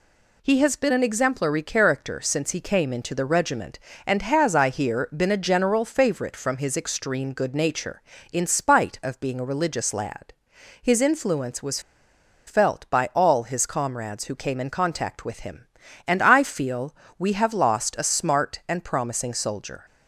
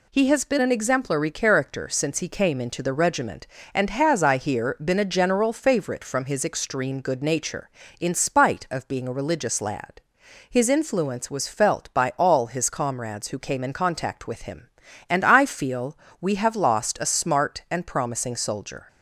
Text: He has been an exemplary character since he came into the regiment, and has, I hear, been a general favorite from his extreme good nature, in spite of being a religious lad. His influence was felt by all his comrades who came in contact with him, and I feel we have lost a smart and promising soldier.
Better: second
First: pauses between "was" and "felt"; noticeable; at 11.7 s; 0.67 s long // pauses between "feel" and "we"; slight; at 16.9 s; 0.24 s long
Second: pauses between "feel" and "we"; slight; at 15.9 s; 0.24 s long

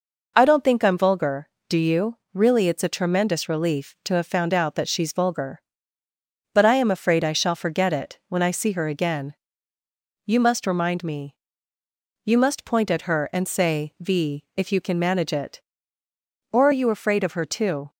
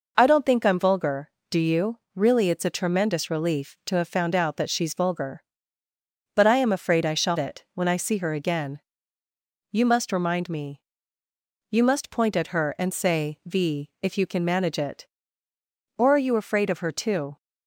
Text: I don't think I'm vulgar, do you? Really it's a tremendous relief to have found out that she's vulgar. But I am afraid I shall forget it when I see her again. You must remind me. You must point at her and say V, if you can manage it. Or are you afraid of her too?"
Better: first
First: none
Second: skips "forget"; at 7.3 s

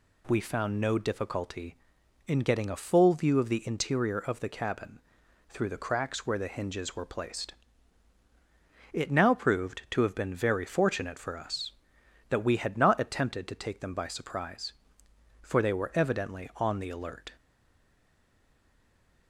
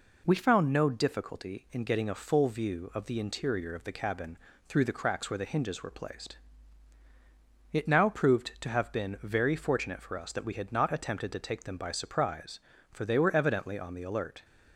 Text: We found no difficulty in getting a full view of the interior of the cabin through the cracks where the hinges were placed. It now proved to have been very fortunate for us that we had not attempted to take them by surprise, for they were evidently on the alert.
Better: second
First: pauses between "cabin" and "through"; noticeable; at 4.9 s; 0.50 s long // stays silent after the last word; noticeable; from 17.3 s on; 1.9 s long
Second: pauses between "cabin" and "through"; slight; at 4.3 s; 0.30 s long

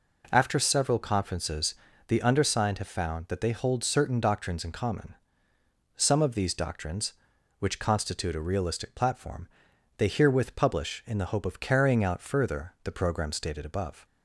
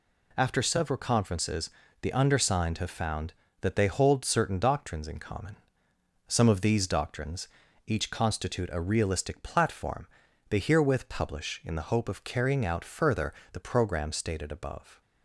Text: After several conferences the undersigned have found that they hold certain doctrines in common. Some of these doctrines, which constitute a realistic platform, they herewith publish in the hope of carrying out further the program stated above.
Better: first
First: pauses between "conferences" and "the"; slight; at 1.7 s; 0.32 s long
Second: pauses between "conferences" and "the"; slight; at 1.6 s; 0.32 s long // says "each" for "which"; at 7.8 s // pauses between "further" and "the"; slight; at 13.3 s; 0.18 s long

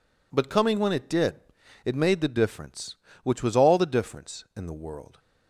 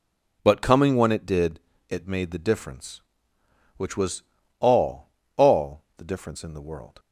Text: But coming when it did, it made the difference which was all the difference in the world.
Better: first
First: none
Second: pauses between "was" and "all"; slight; at 4.2 s; 0.36 s long // says "all" twice; at 5.3 s

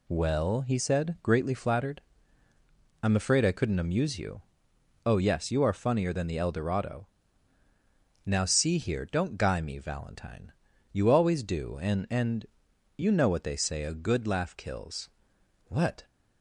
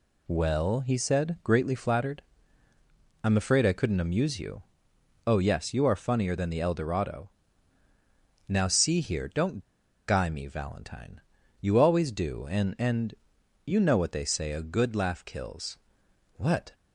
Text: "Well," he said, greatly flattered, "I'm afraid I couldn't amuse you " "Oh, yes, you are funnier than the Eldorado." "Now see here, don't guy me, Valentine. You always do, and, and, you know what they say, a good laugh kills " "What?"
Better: first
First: none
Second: pauses between "don't" and "guy"; noticeable; at 9.5 s; 0.47 s long

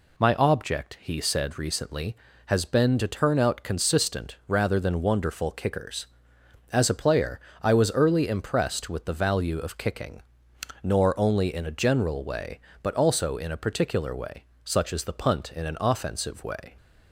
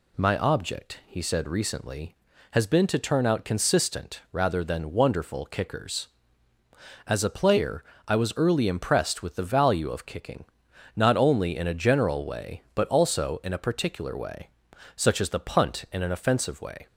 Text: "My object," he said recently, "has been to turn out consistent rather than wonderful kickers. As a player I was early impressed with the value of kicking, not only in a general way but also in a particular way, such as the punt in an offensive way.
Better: second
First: pauses between "player" and "I"; slight; at 7.4 s; 0.22 s long // says "nor" for "not"; at 10.8 s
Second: pauses between "player" and "I"; slight; at 7.8 s; 0.24 s long

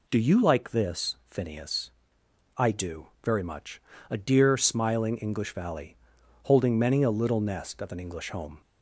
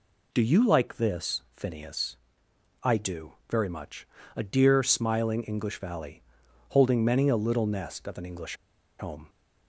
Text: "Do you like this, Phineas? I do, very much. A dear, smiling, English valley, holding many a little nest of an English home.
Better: first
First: none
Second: pauses between "English" and "home"; at 8.5 s; 0.44 s long

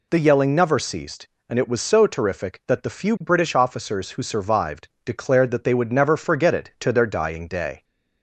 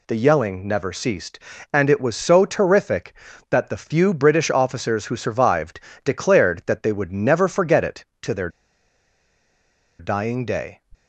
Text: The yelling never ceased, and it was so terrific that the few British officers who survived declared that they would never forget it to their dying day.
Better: first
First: pauses between "survived" and "declared"; slight; at 4.8 s; 0.16 s long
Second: pauses between "survived" and "declared"; slight; at 5.7 s; 0.24 s long // pauses between "their" and "dying"; strong; at 8.4 s; 1.5 s long

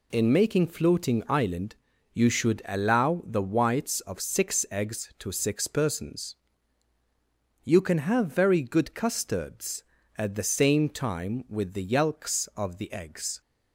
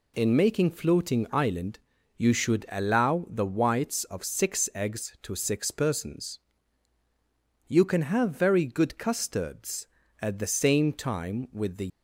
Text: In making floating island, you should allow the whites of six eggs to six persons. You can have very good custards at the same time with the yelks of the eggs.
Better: first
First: none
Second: stops before "yelks of the eggs"; at 11.8 s

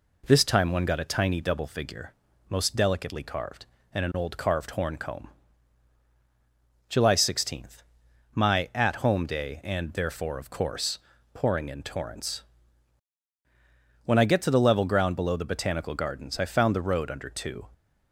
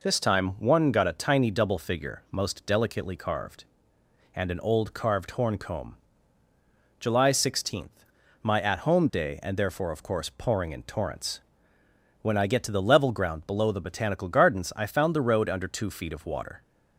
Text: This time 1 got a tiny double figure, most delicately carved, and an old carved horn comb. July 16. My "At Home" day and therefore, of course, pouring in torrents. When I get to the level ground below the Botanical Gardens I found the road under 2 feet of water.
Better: second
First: stops before "feet of water"; at 17.7 s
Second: none

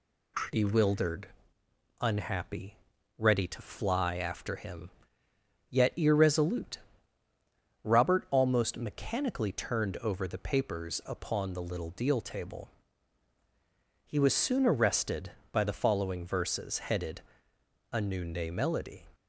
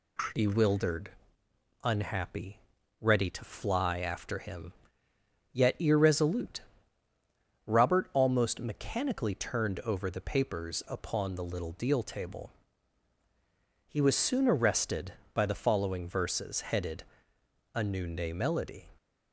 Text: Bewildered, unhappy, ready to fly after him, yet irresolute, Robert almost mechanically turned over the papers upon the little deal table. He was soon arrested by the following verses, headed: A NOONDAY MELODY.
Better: neither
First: none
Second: none

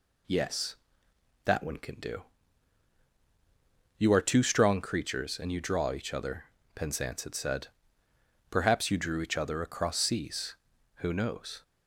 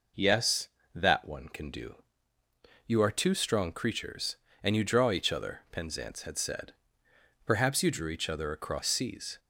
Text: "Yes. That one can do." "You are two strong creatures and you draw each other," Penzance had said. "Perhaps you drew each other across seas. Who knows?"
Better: first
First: none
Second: stops before "Who knows"; at 9.3 s

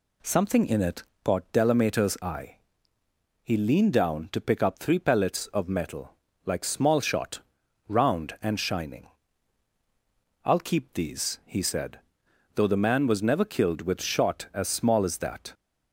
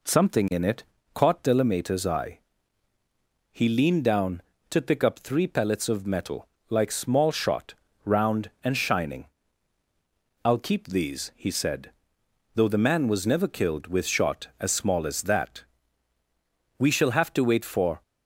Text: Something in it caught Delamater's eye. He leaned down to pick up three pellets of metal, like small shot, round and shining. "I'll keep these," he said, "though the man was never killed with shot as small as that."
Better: first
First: pauses between "it" and "caught"; slight; at 1.0 s; 0.20 s long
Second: pauses between "it" and "caught"; slight; at 0.8 s; 0.30 s long // goes on to say "We shall have to wait for"; noticeable; from 16.7 s on; 1.2 s long

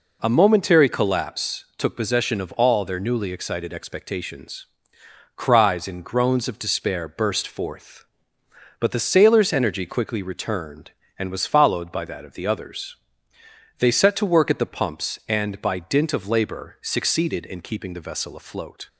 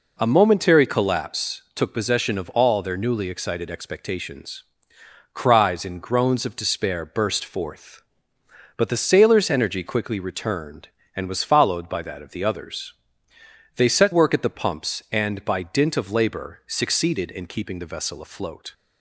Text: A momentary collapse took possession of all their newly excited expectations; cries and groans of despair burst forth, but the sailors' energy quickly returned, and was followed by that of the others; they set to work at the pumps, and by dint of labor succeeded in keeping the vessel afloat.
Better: first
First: none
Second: skips "to"; at 14.1 s

